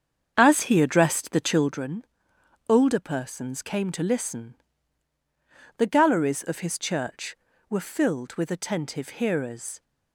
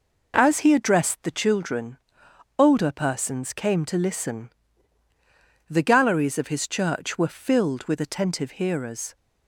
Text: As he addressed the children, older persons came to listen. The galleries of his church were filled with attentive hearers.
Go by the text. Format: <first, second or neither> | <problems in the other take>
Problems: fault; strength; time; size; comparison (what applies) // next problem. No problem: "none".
second | starts louder than the rest; strong; until 1.8 s; 7.5 dB